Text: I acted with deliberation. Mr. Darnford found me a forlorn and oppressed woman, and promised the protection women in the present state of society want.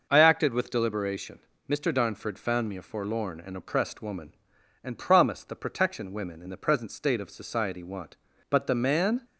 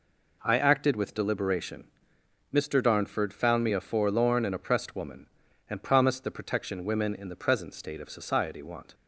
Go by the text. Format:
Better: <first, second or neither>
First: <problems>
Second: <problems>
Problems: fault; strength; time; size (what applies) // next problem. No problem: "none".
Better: second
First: goes on to say "But the man"; noticeable; from 8.4 s on; 0.72 s long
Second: none